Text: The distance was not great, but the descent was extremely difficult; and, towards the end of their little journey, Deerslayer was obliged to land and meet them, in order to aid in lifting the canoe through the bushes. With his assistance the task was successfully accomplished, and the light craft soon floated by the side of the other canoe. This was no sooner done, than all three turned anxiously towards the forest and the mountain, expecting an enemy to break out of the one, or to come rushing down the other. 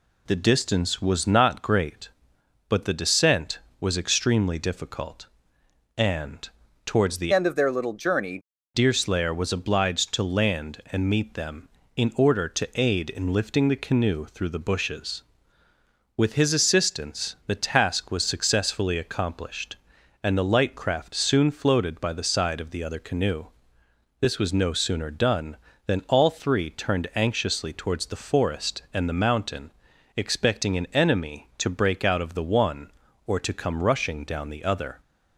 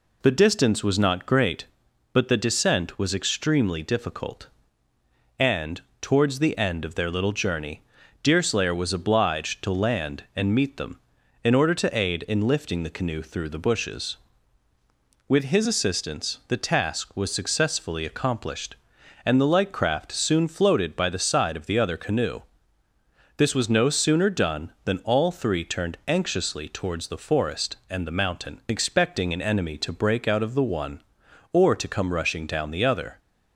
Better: second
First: changes voice from "end" to "journey"; from 7.3 to 8.3 s; 1.0 s long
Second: none

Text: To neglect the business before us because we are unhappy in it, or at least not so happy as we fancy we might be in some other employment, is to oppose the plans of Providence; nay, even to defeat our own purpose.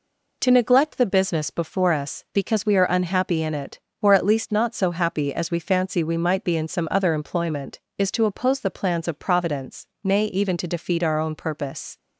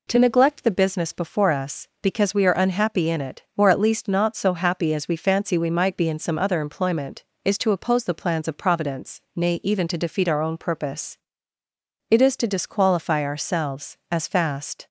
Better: first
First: none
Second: goes on to say "It is to disqualify ourselves as fast"; strong; from 12.0 s on; 2.7 s long

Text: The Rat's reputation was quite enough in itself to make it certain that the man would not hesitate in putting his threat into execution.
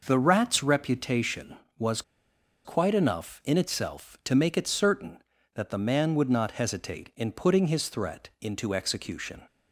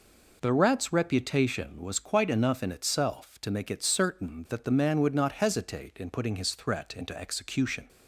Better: second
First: pauses between "was" and "quite"; noticeable; at 2.0 s; 0.63 s long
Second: none

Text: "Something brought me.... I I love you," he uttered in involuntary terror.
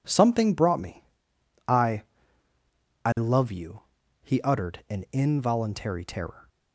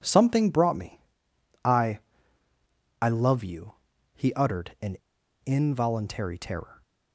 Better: first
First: pauses between "I" and "I"; at 2.0 s; 1.0 s long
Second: pauses between "I" and "I"; at 2.0 s; 1.0 s long // pauses between "in" and "involuntary"; noticeable; at 4.9 s; 0.47 s long

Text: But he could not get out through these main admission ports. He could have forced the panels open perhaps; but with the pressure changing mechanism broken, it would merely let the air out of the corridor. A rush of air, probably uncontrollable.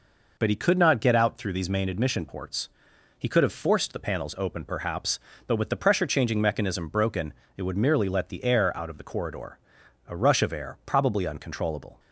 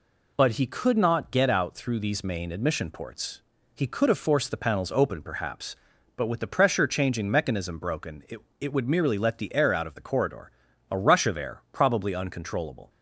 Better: first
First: none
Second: says "it" twice; at 8.5 s

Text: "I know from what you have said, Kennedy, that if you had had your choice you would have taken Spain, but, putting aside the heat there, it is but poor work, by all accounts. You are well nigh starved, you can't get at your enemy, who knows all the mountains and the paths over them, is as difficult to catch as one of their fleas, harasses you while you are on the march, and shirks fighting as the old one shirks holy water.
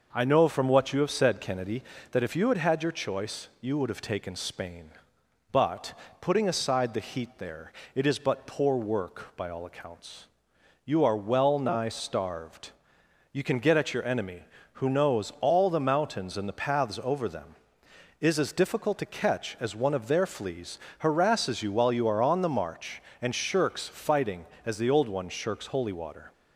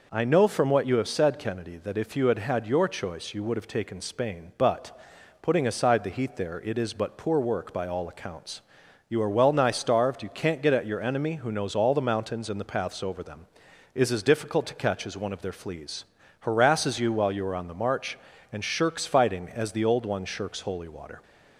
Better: second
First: says "can" for "can't"; at 13.4 s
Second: none

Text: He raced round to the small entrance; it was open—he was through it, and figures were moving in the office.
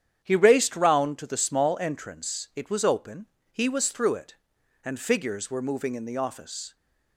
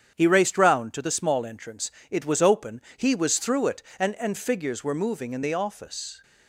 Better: first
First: starts louder than the rest; strong; until 1.2 s; 9 dB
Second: starts louder than the rest; strong; until 1.1 s; 8.5 dB // says "and" twice; at 4.1 s

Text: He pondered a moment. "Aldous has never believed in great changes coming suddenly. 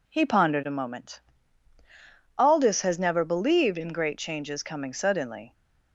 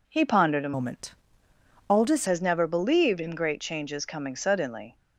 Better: first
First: none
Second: changes voice from "moment" to "Aldous"; from 0.7 to 2.2 s; 1.5 s long

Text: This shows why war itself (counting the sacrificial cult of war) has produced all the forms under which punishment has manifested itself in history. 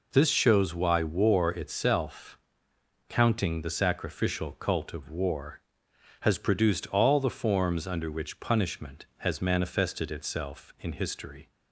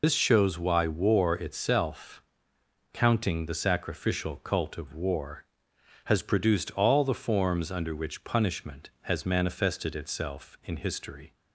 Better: first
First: none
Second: loses the start of "This"; at 0.0 s; 70 ms

